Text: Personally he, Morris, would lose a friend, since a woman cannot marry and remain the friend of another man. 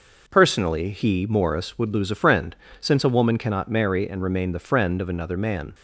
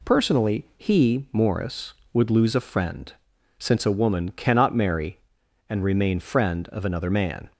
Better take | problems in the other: first | skips "the"; at 6.1 s

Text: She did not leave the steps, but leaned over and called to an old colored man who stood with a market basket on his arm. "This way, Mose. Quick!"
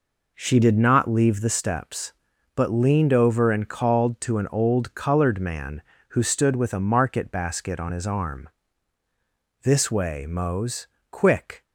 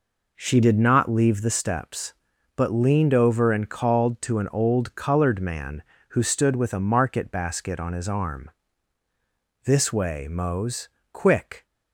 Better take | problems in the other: neither | none

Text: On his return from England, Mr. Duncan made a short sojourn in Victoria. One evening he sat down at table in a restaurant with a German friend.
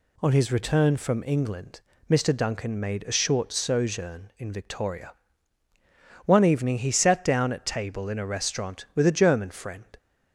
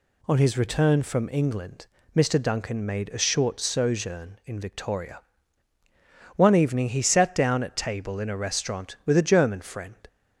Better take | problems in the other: neither | none

